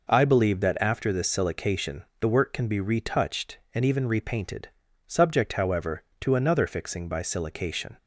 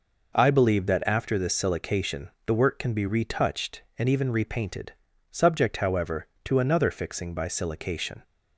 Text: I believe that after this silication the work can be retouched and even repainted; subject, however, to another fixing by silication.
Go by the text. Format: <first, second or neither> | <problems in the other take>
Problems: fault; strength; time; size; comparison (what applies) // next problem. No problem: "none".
neither | pauses between "silication" and "the"; slight; the same in both